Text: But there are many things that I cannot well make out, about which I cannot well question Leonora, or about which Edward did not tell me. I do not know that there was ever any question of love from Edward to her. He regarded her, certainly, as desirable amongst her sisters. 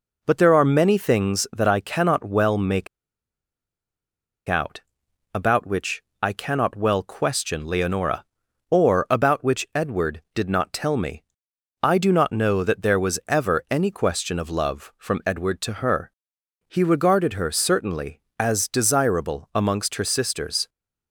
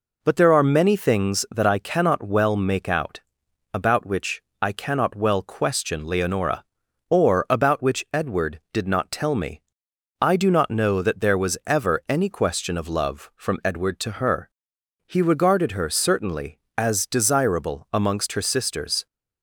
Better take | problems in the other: second | pauses between "make" and "out"; strong; at 2.8 s; 1.6 s long // pauses between "which" and "I"; slight; at 6.0 s; 0.18 s long; slight in the second

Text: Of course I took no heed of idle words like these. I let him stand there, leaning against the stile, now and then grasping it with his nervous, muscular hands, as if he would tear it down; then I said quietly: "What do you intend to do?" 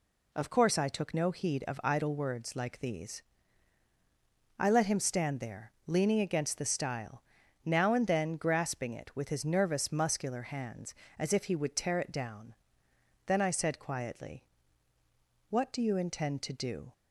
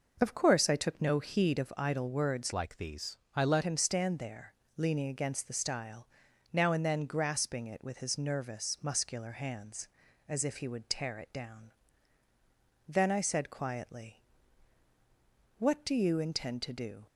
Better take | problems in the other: first | changes voice from "like" to "let"; from 2.5 to 3.6 s; 1.1 s long

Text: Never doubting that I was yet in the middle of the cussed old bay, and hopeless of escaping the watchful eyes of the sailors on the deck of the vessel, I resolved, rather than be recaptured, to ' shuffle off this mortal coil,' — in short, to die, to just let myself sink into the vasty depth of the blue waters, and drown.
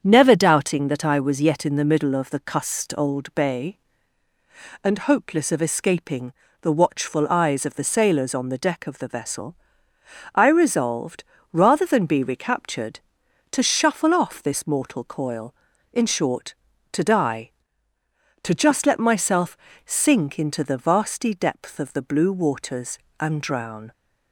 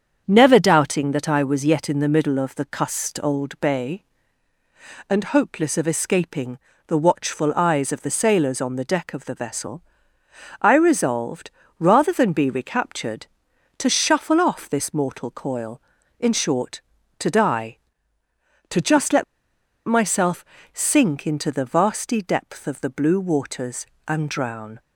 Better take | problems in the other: first | starts louder than the rest; strong; until 1.2 s; 7.5 dB; strong in the first // pauses between "escaping" and "the"; slight; at 6.5 s; 0.30 s long; slight in the first // pauses between "let" and "myself"; noticeable; at 19.2 s; 0.62 s long // pauses between "myself" and "sink"; slight; at 20.4 s; 0.26 s long; slight in the first

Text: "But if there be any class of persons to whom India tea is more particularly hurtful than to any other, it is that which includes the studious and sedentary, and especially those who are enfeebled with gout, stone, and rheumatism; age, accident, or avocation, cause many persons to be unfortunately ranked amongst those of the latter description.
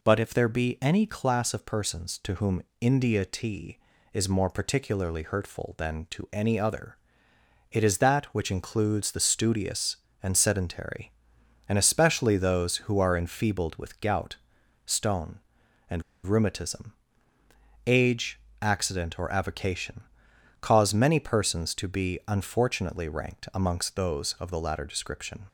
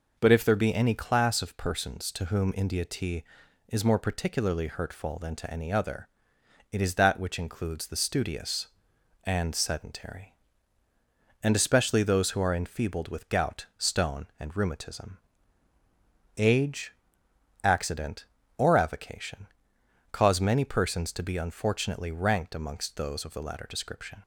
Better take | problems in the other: second | pauses between "whom" and "India"; slight; at 2.6 s; 0.18 s long // pauses between "and" and "rheumatism"; slight; at 16.0 s; 0.21 s long

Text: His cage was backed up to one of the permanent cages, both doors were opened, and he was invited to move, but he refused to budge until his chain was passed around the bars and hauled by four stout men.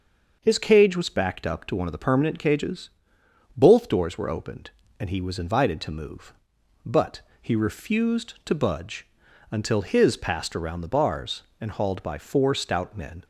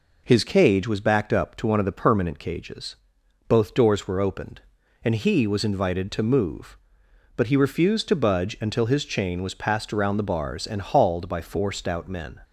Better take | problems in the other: second | starts louder than the rest; until 1.4 s; 6 dB // pauses between "but" and "he"; slight; at 7.2 s; 0.20 s long // pauses between "budge" and "until"; at 9.0 s; 0.44 s long // skips "chain was"; at 10.1 s

